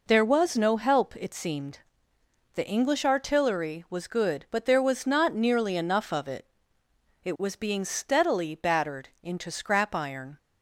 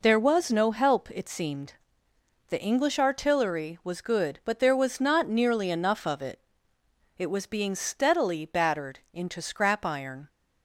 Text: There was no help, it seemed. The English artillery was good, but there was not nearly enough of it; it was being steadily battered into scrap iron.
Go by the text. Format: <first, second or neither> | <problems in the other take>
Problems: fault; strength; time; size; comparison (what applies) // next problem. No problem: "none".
neither | pauses between "battered" and "into"; slight; the same in both